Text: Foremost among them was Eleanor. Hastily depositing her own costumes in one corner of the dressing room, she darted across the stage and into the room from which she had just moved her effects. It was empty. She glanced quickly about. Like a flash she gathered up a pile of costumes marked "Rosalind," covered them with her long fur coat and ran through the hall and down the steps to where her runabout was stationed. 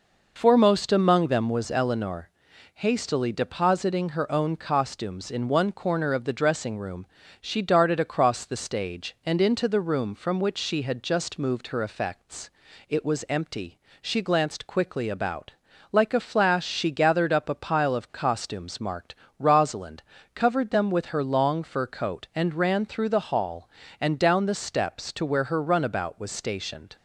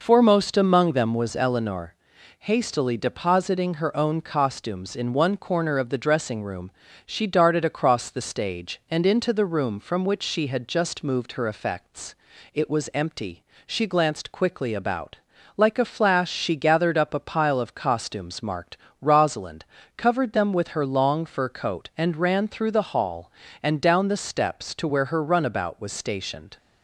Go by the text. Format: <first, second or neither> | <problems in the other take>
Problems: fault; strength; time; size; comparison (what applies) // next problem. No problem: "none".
neither | pauses between "marked" and "Rosalind"; slight; the same in both